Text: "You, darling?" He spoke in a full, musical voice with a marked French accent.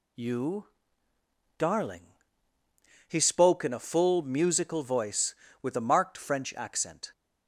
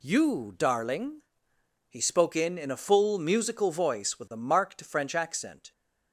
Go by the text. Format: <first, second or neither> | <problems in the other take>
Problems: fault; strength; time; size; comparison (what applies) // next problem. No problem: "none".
first | says "in" twice; at 2.5 s